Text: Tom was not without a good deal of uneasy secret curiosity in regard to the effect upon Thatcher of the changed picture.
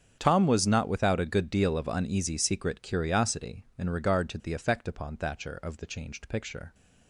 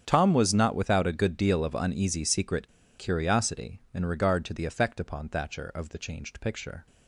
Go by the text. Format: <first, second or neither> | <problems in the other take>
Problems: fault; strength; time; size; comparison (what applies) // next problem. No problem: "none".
first | starts louder than the rest; strong; until 1.0 s; 8 dB; strong in the first // pauses between "secret" and "curiosity"; slight; at 2.6 s; 0.29 s long